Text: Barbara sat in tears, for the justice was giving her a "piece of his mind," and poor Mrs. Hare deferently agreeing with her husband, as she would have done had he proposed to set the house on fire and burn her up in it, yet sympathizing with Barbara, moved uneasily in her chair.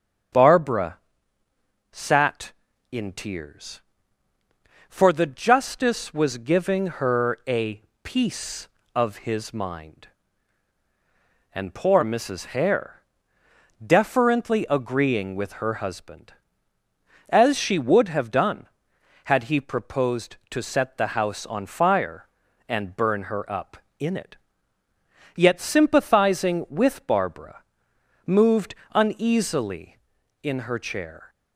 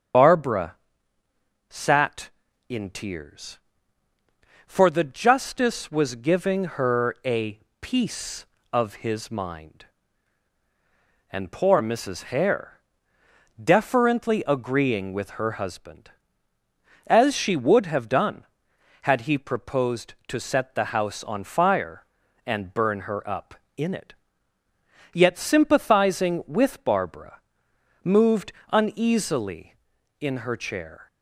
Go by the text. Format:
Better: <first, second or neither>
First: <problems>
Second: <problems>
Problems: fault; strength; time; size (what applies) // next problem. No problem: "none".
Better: first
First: starts louder than the rest; strong; until 2.2 s; 8 dB // pauses between "Barbara" and "sat"; noticeable; at 0.9 s; 0.94 s long // pauses between "a" and "piece"; slight; at 7.8 s; 0.20 s long // pauses between "Hare" and "deferently"; noticeable; at 13.0 s; 0.76 s long // pauses between "moved" and "uneasily"; slight; at 28.7 s; 0.20 s long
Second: loses the start of "Barbara"; at 0.1 s; 35 ms // starts louder than the rest; strong; until 2.0 s; 8 dB // pauses between "Barbara" and "sat"; noticeable; at 0.7 s; 0.94 s long // pauses between "a" and "piece"; slight; at 7.5 s; 0.20 s long // pauses between "Hare" and "deferently"; noticeable; at 12.8 s; 0.76 s long // pauses between "moved" and "uneasily"; slight; at 28.5 s; 0.20 s long